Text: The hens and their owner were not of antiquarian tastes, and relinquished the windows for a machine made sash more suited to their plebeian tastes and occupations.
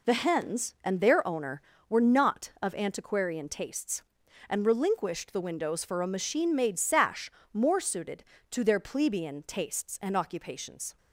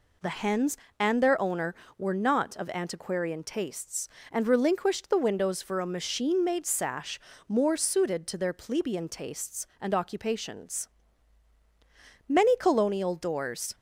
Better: first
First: pauses between "sash" and "more"; slight; at 7.3 s; 0.22 s long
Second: pauses between "sash" and "more"; slight; at 7.1 s; 0.28 s long // goes on to say "Many colonial doors"; from 12.2 s on; 1.4 s long

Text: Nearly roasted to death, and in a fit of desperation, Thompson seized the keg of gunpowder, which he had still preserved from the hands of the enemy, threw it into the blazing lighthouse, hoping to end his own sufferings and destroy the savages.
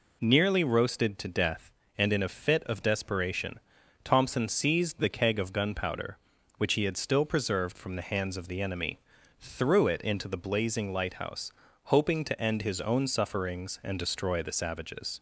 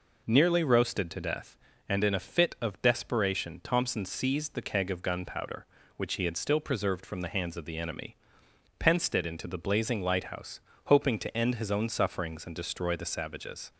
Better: first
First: none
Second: says "pensed" for "threw"; at 8.7 s

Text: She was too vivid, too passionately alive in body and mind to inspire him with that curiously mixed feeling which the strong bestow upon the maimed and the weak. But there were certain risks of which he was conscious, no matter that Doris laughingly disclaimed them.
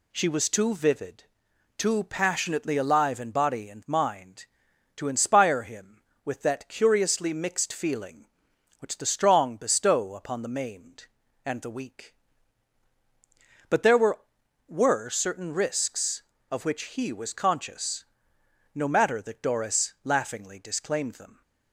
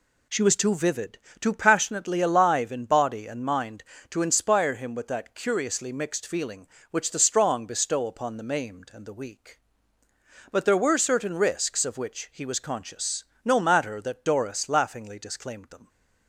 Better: second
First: says "were" twice; at 14.6 s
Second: none

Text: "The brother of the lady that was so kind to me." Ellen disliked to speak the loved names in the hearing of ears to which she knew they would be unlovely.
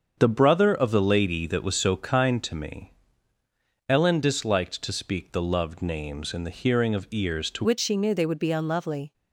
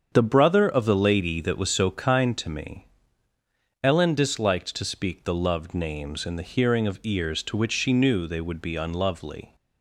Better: second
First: starts louder than the rest; until 1.1 s; 7 dB // changes voice at "which"; from 7.6 s on; 1.5 s long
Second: starts louder than the rest; strong; until 1.1 s; 7 dB

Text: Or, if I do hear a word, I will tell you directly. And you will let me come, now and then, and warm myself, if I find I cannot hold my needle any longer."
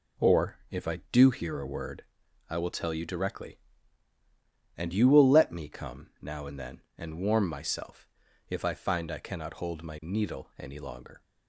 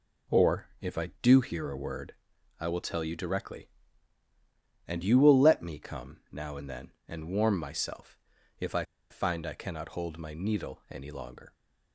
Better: first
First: none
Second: pauses between "I" and "find"; slight; at 8.8 s; 0.25 s long

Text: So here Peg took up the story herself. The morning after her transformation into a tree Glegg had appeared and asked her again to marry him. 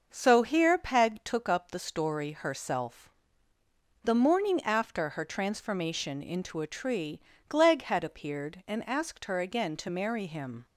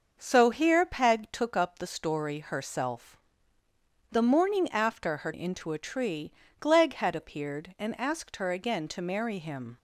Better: first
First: starts louder than the rest; until 1.1 s; 6 dB // pauses between "tree" and "Glegg"; slight; at 7.2 s; 0.28 s long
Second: starts louder than the rest; until 1.2 s; 6 dB // skips "transformation"; at 5.3 s // pauses between "tree" and "Glegg"; slight; at 6.3 s; 0.28 s long

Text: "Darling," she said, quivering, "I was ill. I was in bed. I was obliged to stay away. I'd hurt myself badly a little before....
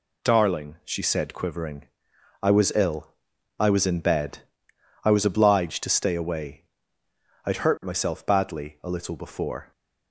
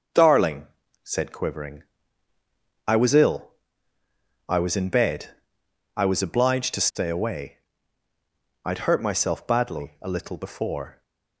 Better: first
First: none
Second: starts louder than the rest; noticeable; until 1.5 s; 6 dB // skips "she"; at 0.8 s

